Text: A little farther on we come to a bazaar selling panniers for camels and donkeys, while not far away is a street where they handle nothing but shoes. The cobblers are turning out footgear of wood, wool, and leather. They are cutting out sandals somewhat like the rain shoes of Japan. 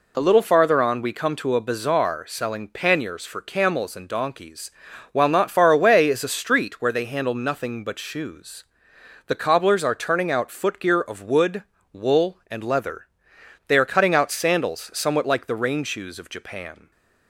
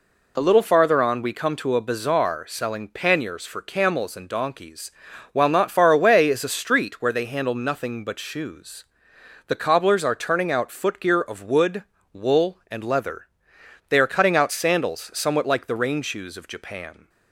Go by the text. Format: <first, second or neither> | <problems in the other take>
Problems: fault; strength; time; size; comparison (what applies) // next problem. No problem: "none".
neither | none